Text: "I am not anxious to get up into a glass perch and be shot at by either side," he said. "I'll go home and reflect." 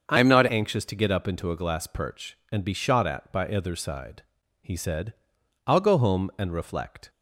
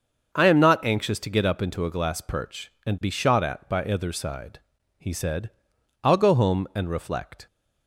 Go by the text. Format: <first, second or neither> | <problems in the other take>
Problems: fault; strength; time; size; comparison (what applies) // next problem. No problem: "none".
second | starts louder than the rest; until 1.1 s; 6.5 dB; also in the second // changes voice from "am" to "not"; from 0.1 to 0.4 s; 0.3 s long